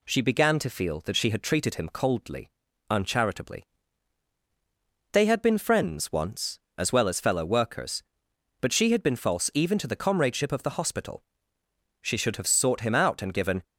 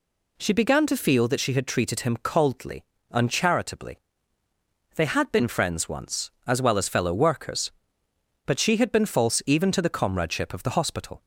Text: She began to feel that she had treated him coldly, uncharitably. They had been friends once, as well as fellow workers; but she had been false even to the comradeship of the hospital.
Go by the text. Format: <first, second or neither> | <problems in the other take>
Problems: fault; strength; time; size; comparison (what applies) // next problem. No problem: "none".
second | goes on to say "She should have sought him out and given"; from 12.0 s on; 1.6 s long